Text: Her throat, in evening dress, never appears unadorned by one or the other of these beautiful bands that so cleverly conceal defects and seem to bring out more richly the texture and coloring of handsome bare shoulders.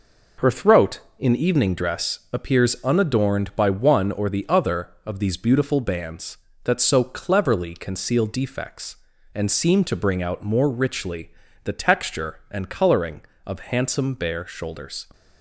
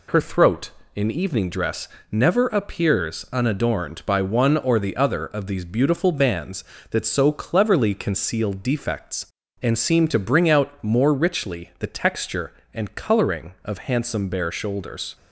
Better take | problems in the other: second | skips "never"; at 2.2 s // pauses between "richly" and "the"; slight; at 11.3 s; 0.34 s long

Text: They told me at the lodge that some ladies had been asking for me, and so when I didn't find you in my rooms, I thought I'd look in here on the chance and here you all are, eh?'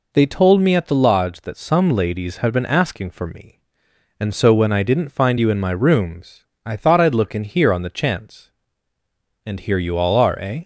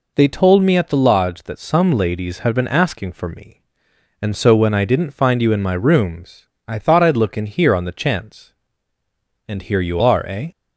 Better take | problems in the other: first | skips "all"; at 10.0 s

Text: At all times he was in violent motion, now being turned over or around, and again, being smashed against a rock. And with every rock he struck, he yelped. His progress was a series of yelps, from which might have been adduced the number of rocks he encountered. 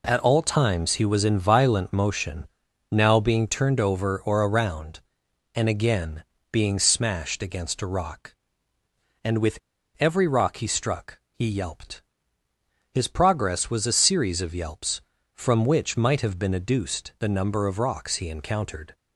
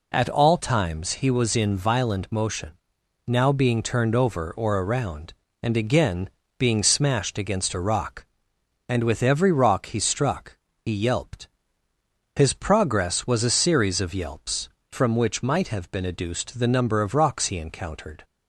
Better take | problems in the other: second | pauses between "with" and "every"; at 9.5 s; 0.42 s long

